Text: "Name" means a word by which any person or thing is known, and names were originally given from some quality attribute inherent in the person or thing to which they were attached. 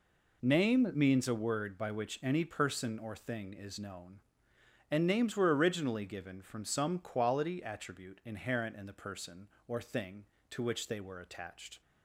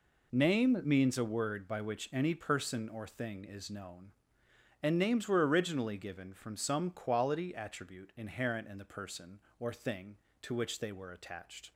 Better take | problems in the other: neither | none

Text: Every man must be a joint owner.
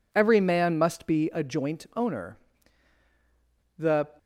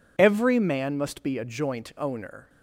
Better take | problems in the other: second | goes on to say "The"; slight; from 3.7 s on; 0.30 s long

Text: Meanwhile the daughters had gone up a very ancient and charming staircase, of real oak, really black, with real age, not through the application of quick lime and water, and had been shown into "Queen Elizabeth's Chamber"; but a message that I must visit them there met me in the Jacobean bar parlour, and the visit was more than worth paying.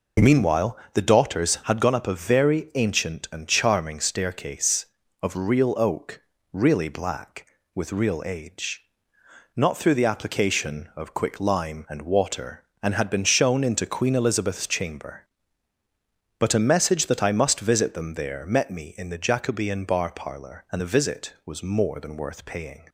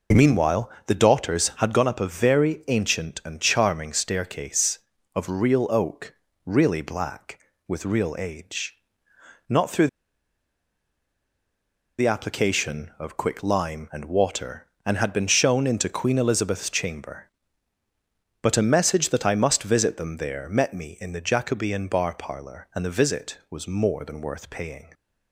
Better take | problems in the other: first | pauses between "Meanwhile" and "the"; slight; at 0.6 s; 0.18 s long; slight in the first // pauses between "through" and "the"; strong; at 9.8 s; 2.1 s long

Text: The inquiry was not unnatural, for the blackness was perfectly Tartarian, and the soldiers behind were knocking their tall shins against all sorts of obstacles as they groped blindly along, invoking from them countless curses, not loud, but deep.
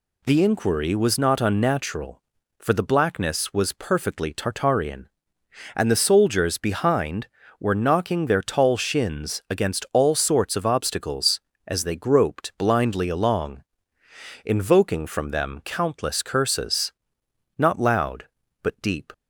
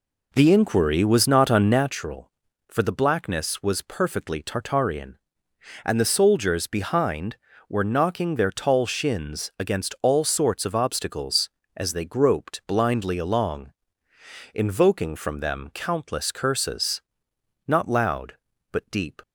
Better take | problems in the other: first | starts louder than the rest; until 1.9 s; 3.5 dB

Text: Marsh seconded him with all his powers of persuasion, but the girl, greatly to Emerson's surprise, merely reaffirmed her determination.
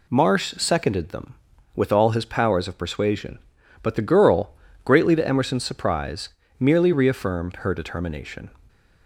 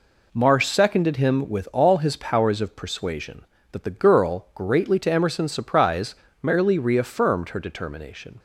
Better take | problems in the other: second | says "them" for "him"; at 1.0 s

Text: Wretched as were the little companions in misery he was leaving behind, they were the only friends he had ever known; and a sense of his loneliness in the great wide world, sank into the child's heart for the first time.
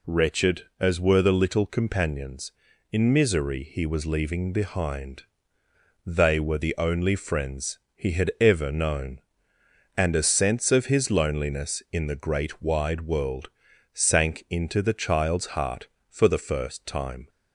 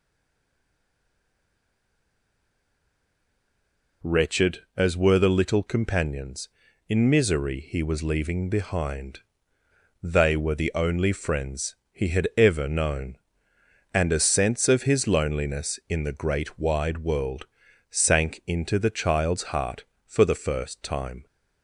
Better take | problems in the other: first | stays silent before the first word; strong; until 4.0 s; 4.0 s long // pauses between "friends" and "he"; slight; at 11.7 s; 0.16 s long; slight in the first

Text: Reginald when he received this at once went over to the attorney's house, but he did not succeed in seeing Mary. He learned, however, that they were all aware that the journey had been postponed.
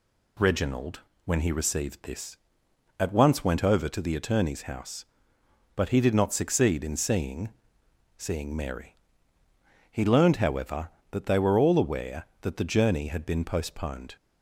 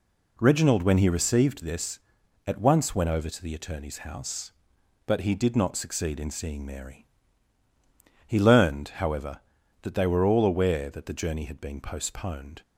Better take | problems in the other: second | pauses between "Reginald" and "when"; slight; at 0.9 s; 0.26 s long // says "seeing" twice; at 8.1 s

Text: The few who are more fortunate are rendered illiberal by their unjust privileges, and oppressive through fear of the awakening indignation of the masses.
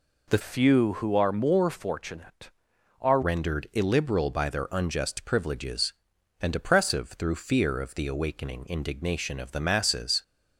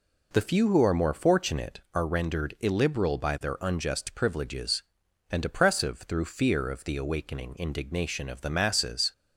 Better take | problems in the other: second | changes voice from "few" to "are"; from 0.4 to 3.2 s; 2.8 s long

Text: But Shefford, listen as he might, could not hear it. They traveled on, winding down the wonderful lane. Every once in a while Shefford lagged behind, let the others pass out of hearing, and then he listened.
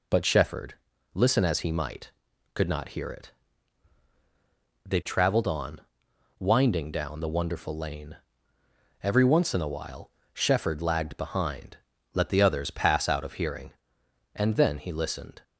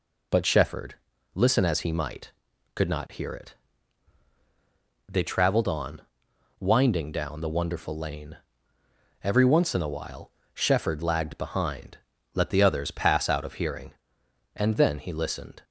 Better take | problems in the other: neither | pauses between "while" and "Shefford"; slight; the same in both

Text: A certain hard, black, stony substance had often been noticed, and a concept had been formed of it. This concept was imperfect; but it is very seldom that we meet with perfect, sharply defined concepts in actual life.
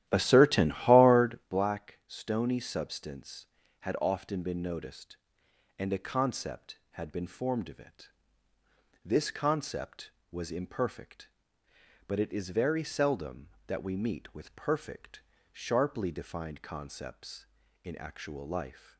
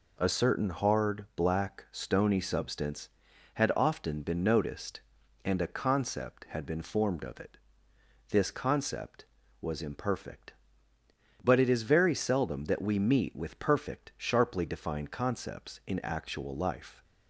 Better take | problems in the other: second | starts louder than the rest; strong; until 1.5 s; 12.5 dB

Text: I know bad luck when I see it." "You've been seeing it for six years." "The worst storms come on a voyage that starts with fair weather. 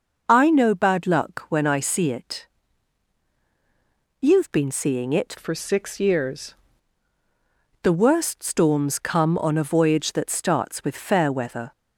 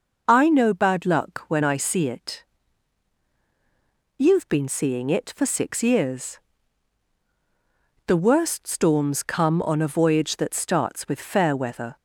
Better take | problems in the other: second | changes voice from "for" to "years"; from 5.3 to 6.5 s; 1.2 s long

